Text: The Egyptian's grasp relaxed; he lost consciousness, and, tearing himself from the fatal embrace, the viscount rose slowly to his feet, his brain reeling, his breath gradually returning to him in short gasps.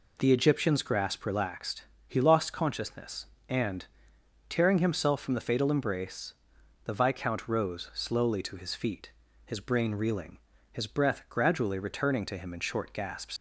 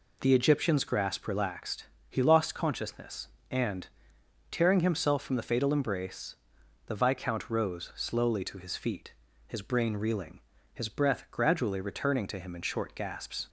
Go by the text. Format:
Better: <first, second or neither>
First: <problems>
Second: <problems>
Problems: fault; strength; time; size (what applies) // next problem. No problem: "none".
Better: second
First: leaves "gasps" unfinished; at 13.3 s; 105 ms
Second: none